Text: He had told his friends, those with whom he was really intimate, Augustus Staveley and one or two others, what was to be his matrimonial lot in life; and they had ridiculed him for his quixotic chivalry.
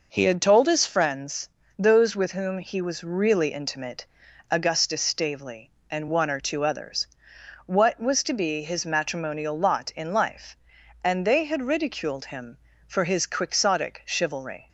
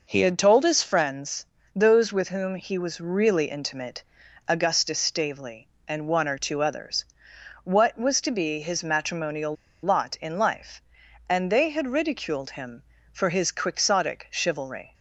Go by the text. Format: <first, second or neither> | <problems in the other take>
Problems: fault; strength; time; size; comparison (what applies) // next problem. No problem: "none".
first | pauses between "matrimonial" and "lot"; slight; at 9.5 s; 0.28 s long